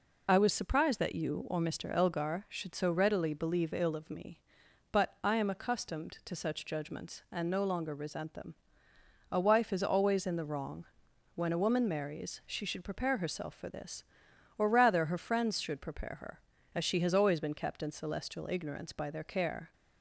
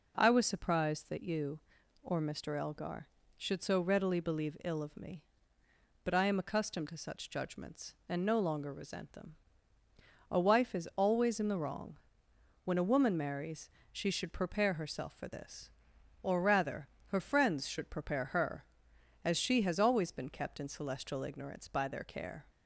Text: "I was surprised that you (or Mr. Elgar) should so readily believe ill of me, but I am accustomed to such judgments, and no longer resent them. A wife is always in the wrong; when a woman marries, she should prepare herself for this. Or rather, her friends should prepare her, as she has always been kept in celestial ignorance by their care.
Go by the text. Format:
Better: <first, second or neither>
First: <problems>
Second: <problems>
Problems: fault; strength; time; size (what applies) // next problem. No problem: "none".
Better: second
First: loses the start of "I"; at 0.2 s; 75 ms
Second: none